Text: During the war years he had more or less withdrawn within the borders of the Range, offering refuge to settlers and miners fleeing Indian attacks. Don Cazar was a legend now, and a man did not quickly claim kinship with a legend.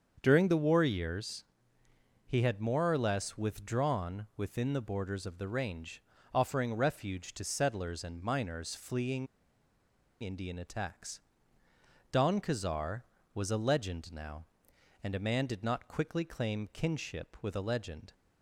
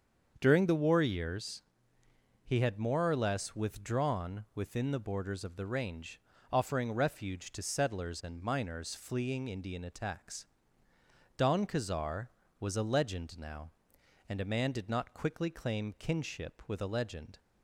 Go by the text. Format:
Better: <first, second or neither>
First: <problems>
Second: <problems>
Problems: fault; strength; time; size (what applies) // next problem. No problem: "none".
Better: second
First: starts louder than the rest; until 1.2 s; 7 dB // pauses between "years" and "he"; noticeable; at 1.4 s; 0.82 s long // pauses between "fleeing" and "Indian"; noticeable; at 9.2 s; 0.96 s long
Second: starts louder than the rest; until 1.3 s; 7 dB // pauses between "years" and "he"; noticeable; at 1.6 s; 0.82 s long